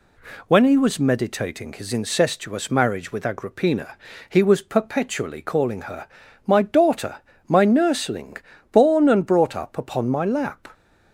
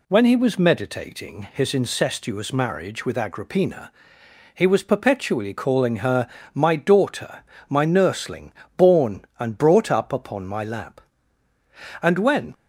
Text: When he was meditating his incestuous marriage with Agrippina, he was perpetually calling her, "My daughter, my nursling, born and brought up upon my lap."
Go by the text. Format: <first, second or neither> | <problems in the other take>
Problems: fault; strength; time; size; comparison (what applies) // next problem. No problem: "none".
first | goes on to say "And when"; from 12.0 s on; 0.50 s long